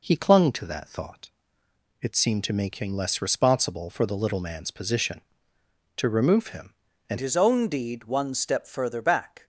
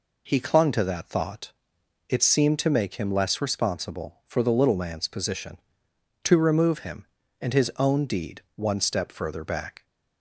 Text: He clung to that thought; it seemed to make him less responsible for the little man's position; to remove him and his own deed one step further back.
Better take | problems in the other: second | changes voice at "his"; from 7.1 s on; 2.3 s long

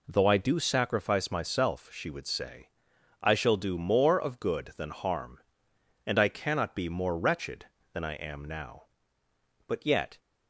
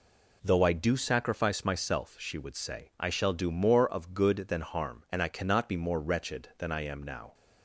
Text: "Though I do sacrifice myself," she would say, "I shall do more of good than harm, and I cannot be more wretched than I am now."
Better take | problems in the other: second | goes on to say "But yet"; from 9.6 s on; 0.52 s long

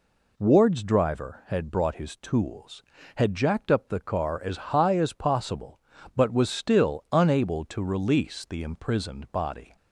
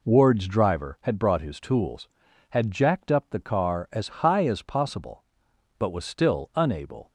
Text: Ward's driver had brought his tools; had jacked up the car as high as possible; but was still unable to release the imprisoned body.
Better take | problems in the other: first | pauses between "as" and "high"; slight; at 4.0 s; 0.16 s long // stops before "to release the imprisoned body"; at 7.0 s

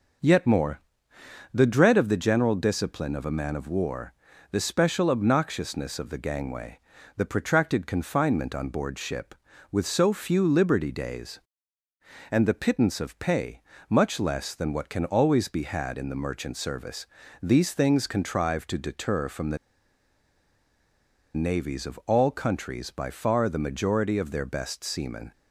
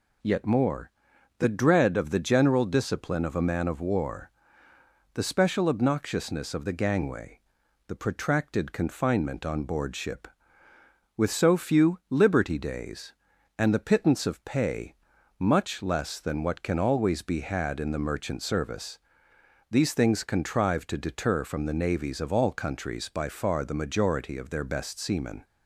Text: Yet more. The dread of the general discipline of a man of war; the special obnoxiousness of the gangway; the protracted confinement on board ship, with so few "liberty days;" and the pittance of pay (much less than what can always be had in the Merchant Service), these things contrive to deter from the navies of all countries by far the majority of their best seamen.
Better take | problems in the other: second | pauses between "the" and "navies"; strong; at 19.5 s; 1.7 s long

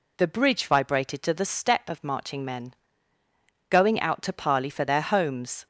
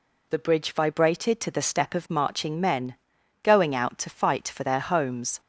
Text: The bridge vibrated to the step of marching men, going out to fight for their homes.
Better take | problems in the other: second | says "parley" for "fight"; at 4.3 s

